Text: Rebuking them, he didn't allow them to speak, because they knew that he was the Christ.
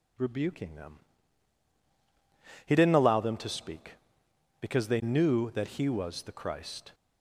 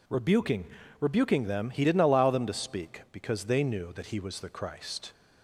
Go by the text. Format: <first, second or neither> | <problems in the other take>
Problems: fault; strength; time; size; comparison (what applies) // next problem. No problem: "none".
first | says "Rebuking" twice; at 0.9 s